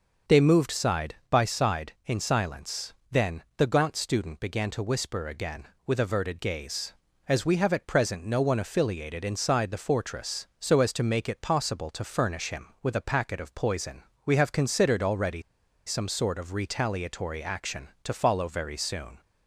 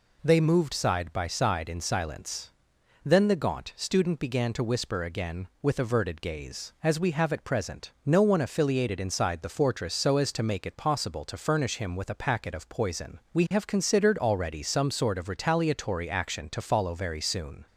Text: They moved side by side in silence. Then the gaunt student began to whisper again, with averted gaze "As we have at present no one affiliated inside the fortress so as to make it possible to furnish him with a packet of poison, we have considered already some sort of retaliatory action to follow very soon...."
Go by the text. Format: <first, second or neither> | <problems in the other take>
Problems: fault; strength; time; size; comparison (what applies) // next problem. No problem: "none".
second | starts louder than the rest; until 1.4 s; 6.5 dB // pauses between "already" and "some"; at 15.4 s; 0.44 s long